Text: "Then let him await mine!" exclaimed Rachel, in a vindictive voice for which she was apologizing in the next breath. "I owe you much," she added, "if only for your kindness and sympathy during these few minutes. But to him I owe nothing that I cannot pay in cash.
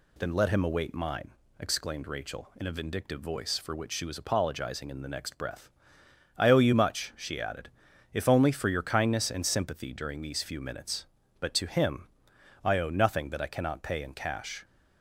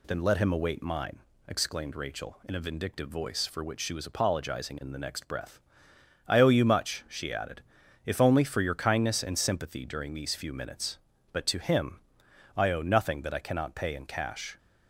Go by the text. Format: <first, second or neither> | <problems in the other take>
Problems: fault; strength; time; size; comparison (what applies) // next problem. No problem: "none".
neither | pauses between "him" and "I"; noticeable; the same in both